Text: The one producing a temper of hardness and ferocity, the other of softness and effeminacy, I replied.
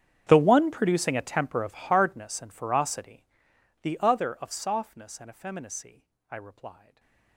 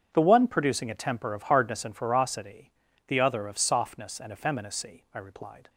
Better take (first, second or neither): second